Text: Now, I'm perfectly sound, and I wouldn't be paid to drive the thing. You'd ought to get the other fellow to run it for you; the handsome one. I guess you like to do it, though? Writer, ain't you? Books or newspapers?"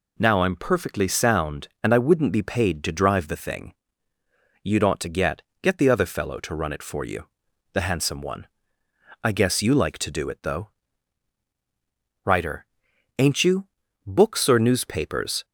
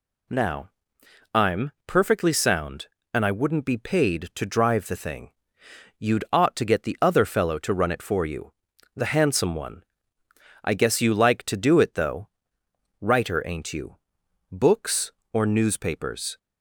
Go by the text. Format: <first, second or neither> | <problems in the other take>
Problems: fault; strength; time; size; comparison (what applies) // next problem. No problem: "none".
second | says "get" twice; at 5.6 s